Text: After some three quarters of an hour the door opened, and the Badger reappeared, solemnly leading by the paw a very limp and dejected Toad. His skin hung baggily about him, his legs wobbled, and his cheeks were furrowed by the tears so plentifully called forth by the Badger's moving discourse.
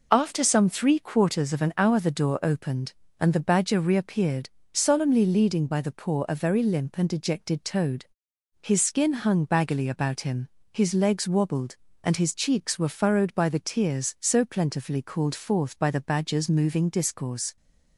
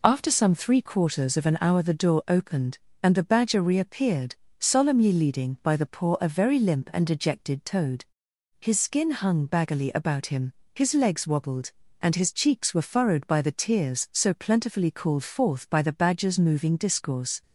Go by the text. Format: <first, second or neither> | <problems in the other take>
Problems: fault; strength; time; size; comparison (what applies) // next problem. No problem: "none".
neither | none